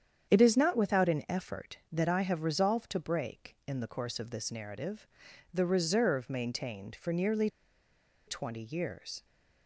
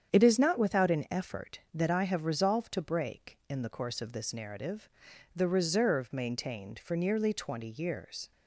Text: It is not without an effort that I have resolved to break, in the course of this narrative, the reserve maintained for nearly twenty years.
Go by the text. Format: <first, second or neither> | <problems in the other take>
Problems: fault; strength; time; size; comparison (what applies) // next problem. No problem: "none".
second | starts louder than the rest; strong; until 1.3 s; 8.5 dB; strong in the second // pauses between "nearly" and "twenty"; noticeable; at 7.4 s; 0.79 s long